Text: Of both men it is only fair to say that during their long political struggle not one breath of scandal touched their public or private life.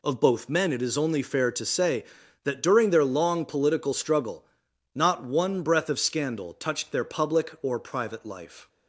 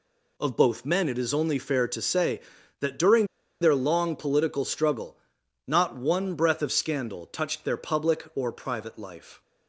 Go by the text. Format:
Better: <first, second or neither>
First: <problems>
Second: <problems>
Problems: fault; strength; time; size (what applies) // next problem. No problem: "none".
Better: first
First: pauses between "struggle" and "not"; noticeable; at 4.4 s; 0.50 s long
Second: pauses between "during" and "their"; at 3.2 s; 0.36 s long // pauses between "struggle" and "not"; noticeable; at 5.1 s; 0.50 s long